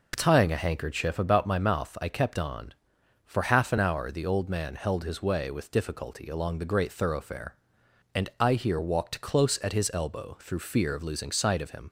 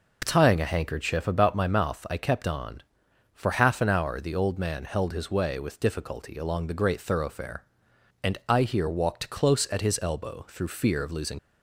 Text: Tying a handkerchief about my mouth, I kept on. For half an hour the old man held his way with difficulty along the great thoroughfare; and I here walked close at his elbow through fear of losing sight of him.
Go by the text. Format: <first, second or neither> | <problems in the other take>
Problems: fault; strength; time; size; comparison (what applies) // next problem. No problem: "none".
first | stops before "sight of him"; at 11.3 s